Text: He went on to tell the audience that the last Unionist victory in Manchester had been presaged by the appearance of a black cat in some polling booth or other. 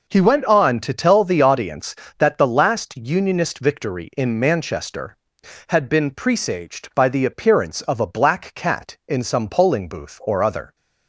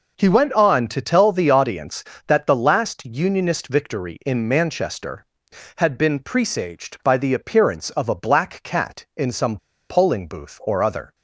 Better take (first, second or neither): first